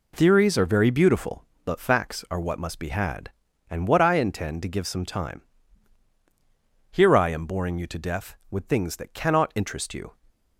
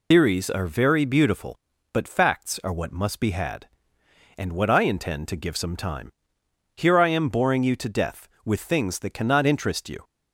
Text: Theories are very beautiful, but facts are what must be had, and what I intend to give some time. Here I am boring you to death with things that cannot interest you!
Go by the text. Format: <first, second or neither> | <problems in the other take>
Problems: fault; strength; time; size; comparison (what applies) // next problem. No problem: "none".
first | loses the start of "Theories"; at 0.1 s; 50 ms